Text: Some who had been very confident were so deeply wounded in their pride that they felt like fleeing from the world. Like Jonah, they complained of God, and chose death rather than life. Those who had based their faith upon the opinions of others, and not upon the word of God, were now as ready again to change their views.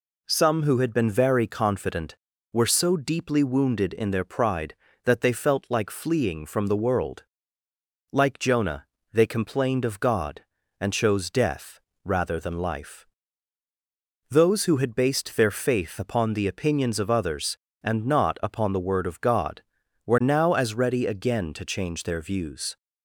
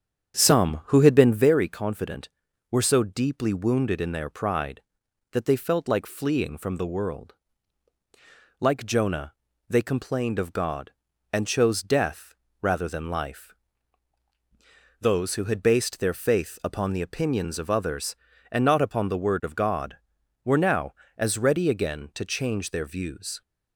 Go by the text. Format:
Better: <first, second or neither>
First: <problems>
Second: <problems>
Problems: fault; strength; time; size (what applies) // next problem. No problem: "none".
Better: first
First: pauses between "death" and "rather"; slight; at 11.7 s; 0.26 s long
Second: starts louder than the rest; strong; until 1.5 s; 8 dB // pauses between "death" and "rather"; slight; at 12.3 s; 0.26 s long